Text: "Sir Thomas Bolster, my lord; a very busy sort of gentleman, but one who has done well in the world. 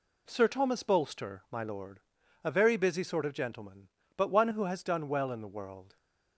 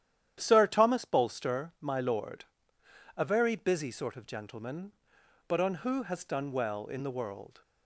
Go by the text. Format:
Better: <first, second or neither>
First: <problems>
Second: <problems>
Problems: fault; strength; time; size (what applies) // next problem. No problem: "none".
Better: first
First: none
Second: starts louder than the rest; strong; until 1.4 s; 10.5 dB // says "on" for "one"; at 5.5 s